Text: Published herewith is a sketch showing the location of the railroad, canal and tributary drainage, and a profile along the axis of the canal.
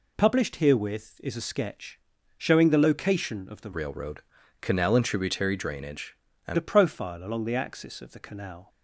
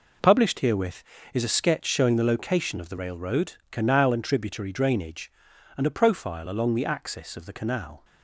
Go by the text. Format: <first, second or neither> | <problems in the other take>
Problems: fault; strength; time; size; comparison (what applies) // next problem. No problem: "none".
second | pauses between "sketch" and "showing"; at 1.9 s; 0.40 s long // changes voice from "railroad" to "and"; from 3.7 to 6.5 s; 2.8 s long